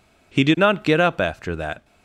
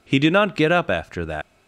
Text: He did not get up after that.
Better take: first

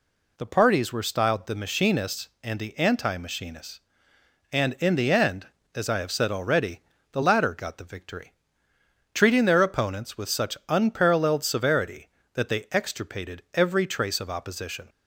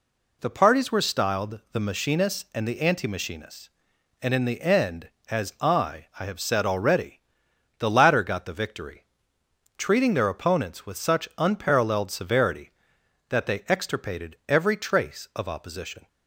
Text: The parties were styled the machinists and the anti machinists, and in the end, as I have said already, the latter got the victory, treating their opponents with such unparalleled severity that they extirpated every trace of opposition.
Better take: first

